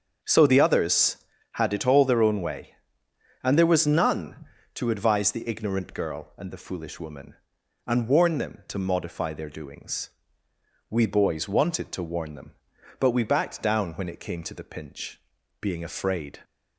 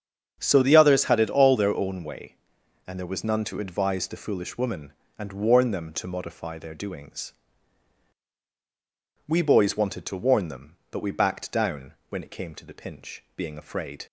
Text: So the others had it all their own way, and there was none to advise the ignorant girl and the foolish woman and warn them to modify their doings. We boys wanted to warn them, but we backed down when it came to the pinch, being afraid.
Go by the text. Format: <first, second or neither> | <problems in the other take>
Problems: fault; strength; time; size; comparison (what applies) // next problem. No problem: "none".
first | starts louder than the rest; strong; until 1.4 s; 7.5 dB; also in the first // skips "the ignorant girl and"; at 4.0 s // pauses between "down" and "when"; slight; at 11.9 s; 0.16 s long